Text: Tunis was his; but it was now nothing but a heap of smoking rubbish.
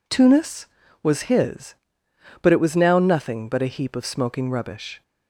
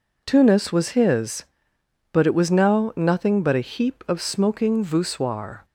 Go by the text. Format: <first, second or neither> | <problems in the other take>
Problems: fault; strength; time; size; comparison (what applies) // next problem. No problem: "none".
first | says "voussoir" for "rubbish"; at 4.8 s